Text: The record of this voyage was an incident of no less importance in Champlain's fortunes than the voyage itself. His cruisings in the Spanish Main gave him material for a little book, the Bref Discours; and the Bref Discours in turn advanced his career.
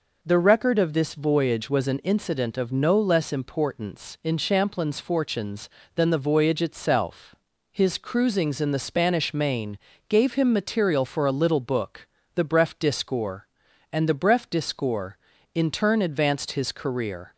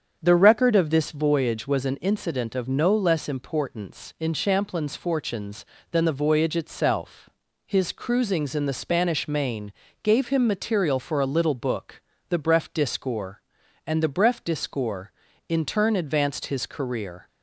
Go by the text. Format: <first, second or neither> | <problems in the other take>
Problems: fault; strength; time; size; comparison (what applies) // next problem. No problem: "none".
first | starts louder than the rest; strong; until 1.4 s; 7.5 dB // pauses between "Main" and "gave"; slight; at 9.7 s; 0.30 s long; slight in the first